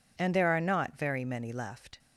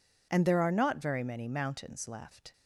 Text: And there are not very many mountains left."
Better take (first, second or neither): second